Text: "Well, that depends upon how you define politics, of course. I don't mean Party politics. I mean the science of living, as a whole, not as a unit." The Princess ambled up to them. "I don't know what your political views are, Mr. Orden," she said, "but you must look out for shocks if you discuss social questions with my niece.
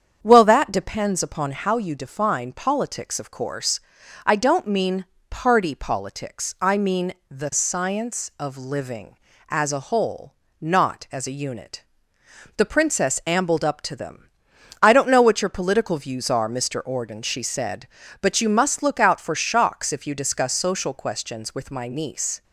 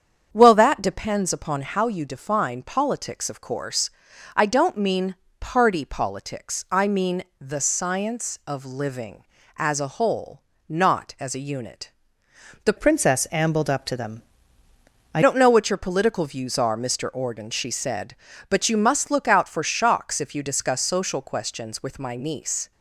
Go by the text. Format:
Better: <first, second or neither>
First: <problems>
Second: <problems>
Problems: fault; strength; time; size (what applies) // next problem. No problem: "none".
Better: first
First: starts louder than the rest; strong; until 1.2 s; 8 dB // pauses between "mean" and "Party"; slight; at 5.0 s; 0.26 s long // pauses between "mean" and "the"; slight; at 7.1 s; 0.18 s long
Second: starts louder than the rest; strong; until 1.3 s; 8 dB // pauses between "mean" and "Party"; slight; at 5.1 s; 0.26 s long // pauses between "mean" and "the"; slight; at 7.2 s; 0.18 s long // changes voice from "Princess" to "I"; from 12.7 to 15.2 s; 2.5 s long